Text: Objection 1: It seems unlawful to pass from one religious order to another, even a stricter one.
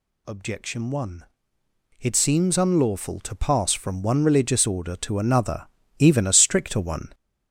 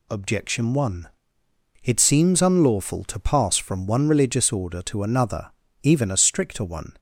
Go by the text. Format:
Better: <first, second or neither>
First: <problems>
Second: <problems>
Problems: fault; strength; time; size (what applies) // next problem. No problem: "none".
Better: second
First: gets louder; noticeable; throughout; 5.5 dB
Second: none